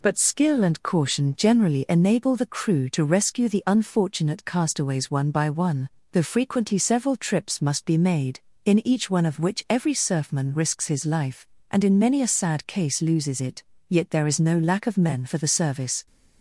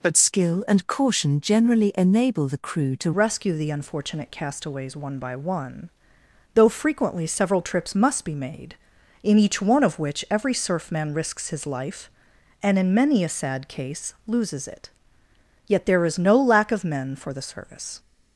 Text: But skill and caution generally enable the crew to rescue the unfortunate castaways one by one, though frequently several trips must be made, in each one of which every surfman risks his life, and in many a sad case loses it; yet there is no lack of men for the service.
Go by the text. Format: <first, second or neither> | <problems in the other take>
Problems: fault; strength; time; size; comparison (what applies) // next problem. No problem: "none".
first | changes voice at "rescue"; from 3.1 s on; 14.8 s long